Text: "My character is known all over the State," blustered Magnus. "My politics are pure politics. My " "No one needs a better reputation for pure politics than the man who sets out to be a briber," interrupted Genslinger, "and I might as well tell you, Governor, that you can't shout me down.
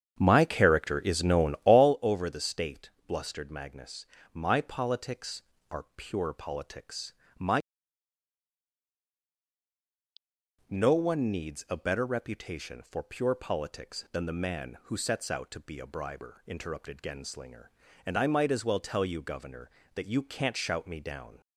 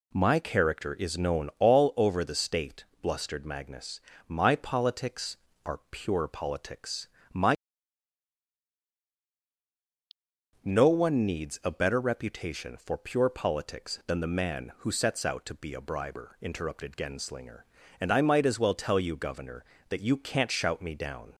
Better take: second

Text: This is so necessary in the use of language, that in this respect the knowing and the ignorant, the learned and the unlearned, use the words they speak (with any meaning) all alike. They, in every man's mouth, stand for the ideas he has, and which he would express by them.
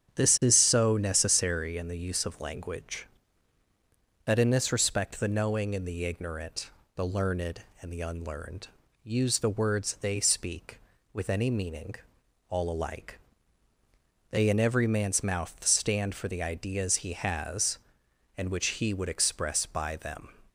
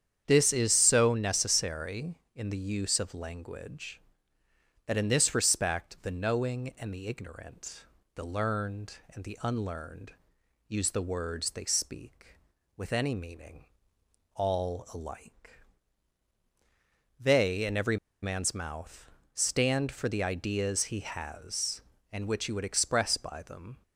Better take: first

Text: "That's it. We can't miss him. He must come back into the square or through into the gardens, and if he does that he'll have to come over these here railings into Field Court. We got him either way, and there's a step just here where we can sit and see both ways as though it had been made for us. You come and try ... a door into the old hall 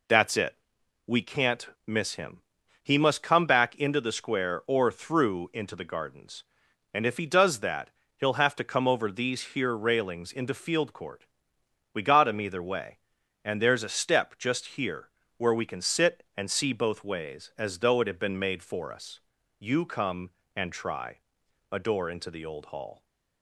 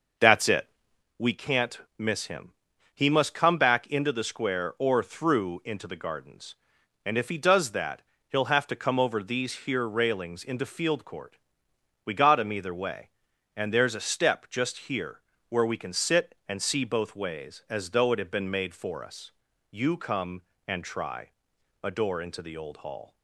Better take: first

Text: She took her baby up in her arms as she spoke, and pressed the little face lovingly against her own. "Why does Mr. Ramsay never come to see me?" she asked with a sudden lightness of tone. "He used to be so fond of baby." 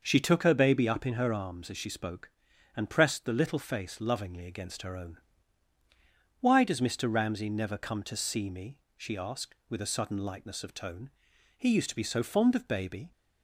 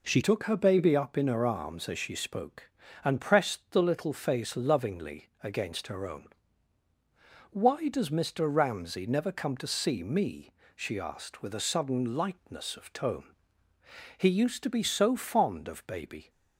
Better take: first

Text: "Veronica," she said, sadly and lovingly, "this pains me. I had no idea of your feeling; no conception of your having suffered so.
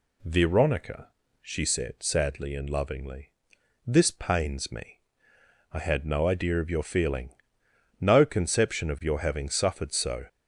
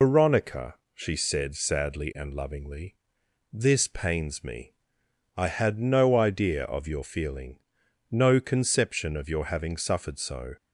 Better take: first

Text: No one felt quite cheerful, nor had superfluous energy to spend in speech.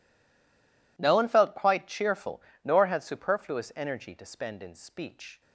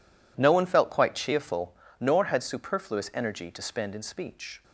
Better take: second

